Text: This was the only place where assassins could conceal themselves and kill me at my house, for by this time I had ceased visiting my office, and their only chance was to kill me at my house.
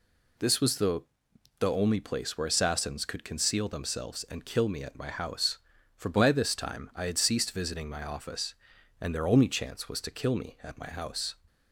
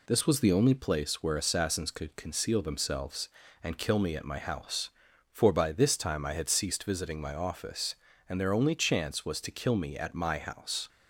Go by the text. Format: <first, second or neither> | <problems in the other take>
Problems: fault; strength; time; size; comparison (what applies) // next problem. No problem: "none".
second | says "the" twice; at 1.5 s